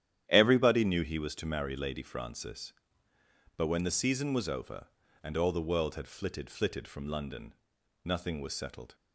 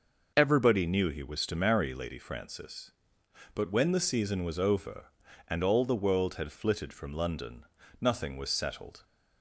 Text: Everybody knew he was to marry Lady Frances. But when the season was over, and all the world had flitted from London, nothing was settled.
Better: second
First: starts louder than the rest; strong; until 1.2 s; 10.5 dB // says "flitted" twice; at 6.4 s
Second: none

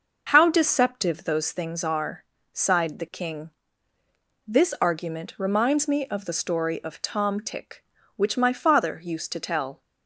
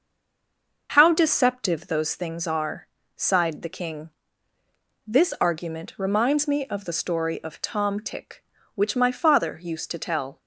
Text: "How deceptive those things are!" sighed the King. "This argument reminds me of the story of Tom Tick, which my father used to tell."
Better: first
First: none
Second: stays silent before the first word; slight; until 0.8 s; 0.8 s long

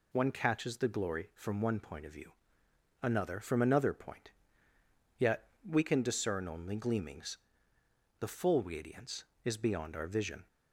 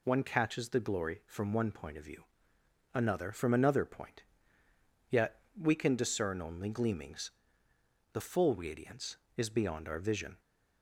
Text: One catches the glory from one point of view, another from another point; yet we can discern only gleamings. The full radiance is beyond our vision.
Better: neither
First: pauses between "yet" and "we"; slight; at 5.4 s; 0.16 s long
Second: pauses between "yet" and "we"; slight; at 5.4 s; 0.16 s long

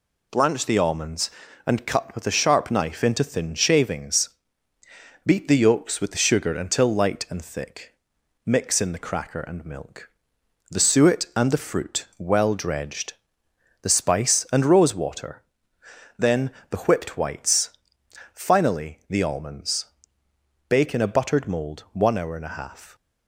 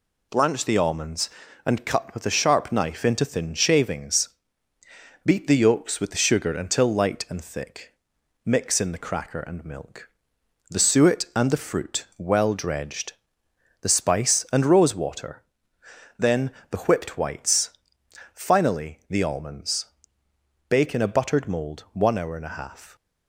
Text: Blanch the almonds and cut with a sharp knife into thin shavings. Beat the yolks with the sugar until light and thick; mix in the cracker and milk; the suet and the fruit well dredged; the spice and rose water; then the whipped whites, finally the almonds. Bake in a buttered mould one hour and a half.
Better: neither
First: pauses between "then" and "the"; slight; at 16.5 s; 0.20 s long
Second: pauses between "then" and "the"; slight; at 16.5 s; 0.20 s long

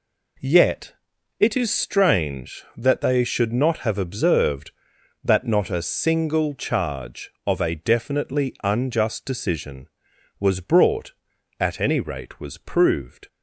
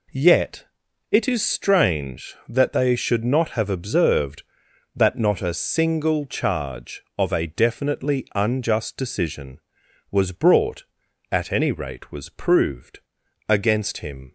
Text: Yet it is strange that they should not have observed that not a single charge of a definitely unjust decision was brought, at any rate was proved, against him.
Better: second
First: pauses between "Yet" and "it"; noticeable; at 0.9 s; 0.46 s long // stops before "against him"; at 13.2 s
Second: pauses between "Yet" and "it"; noticeable; at 0.6 s; 0.46 s long

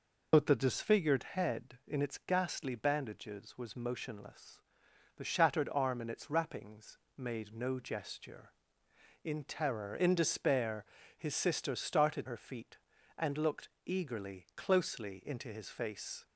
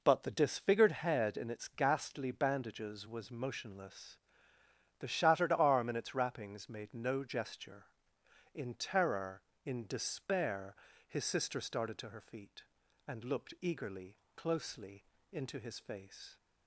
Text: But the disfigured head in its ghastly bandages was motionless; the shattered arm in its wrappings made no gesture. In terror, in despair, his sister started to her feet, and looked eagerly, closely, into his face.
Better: second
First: pauses between "wrappings" and "made"; slight; at 6.9 s; 0.18 s long // skips "to"; at 12.2 s // pauses between "looked" and "eagerly"; slight; at 13.6 s; 0.16 s long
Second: none

